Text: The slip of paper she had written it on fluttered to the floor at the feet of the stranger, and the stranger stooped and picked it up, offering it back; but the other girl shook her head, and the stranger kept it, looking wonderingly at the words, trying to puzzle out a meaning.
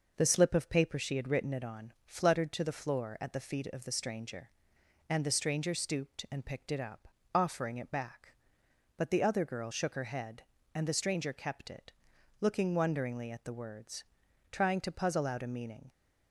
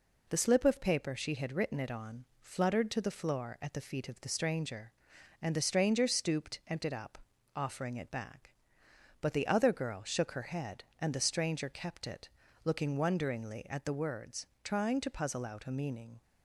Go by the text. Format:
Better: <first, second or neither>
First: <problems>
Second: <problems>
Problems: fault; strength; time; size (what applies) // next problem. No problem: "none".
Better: first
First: none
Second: pauses between "on" and "fluttered"; slight; at 2.2 s; 0.16 s long // skips "picked"; at 6.8 s